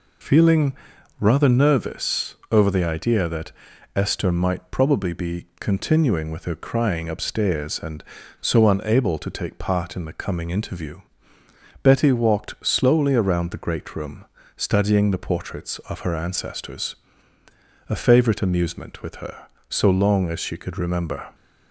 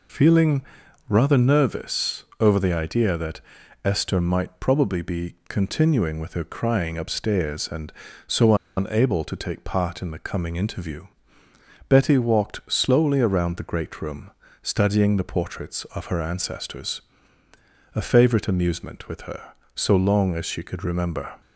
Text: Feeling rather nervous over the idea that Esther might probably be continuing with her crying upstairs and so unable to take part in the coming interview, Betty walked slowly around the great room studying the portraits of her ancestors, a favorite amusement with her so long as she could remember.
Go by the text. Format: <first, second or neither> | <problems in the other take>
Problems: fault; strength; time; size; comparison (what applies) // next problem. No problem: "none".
first | pauses between "Feeling" and "rather"; noticeable; at 0.6 s; 0.46 s long; noticeable in the first // pauses between "nervous" and "over"; slight; at 2.2 s; 0.16 s long; slight in the first // pauses between "that" and "Esther"; noticeable; at 3.3 s; 0.46 s long; noticeable in the first // pauses between "so" and "unable"; slight; at 8.5 s; 0.24 s long // pauses between "room" and "studying"; slight; at 14.3 s; 0.32 s long; slight in the first